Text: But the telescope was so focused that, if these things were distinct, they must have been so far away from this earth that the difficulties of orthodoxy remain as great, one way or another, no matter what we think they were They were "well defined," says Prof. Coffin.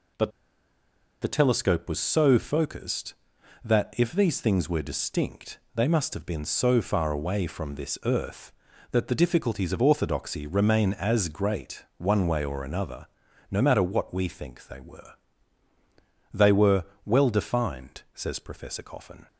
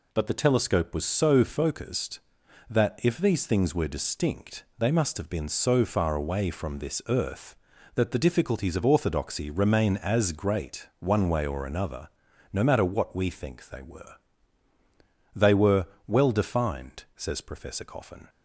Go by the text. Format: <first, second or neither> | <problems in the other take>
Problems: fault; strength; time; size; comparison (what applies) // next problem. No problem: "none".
second | pauses between "But" and "the"; noticeable; at 0.3 s; 0.91 s long // pauses between "were" and "They"; at 15.1 s; 1.1 s long; also in the second // pauses between "were" and "well"; slight; at 16.8 s; 0.20 s long; slight in the second